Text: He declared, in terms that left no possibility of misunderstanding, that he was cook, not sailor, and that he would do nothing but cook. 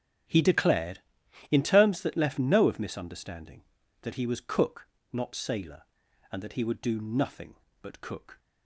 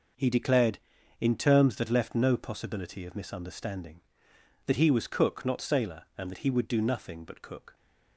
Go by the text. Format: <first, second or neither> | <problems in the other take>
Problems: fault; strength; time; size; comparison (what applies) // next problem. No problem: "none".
second | starts louder than the rest; strong; until 1.7 s; 9.5 dB // skips "possibility"; at 2.6 s